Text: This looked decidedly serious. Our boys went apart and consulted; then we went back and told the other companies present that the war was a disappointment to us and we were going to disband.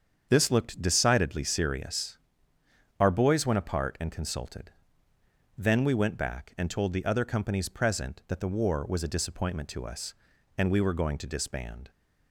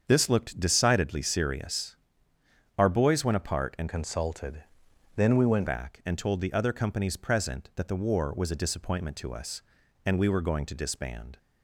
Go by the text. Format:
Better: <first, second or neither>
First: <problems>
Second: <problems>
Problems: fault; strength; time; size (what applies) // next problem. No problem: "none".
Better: first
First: starts louder than the rest; strong; until 1.3 s; 7.5 dB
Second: starts louder than the rest; strong; until 1.0 s; 7 dB // changes voice from "consulted" to "went"; from 3.8 to 5.6 s; 1.8 s long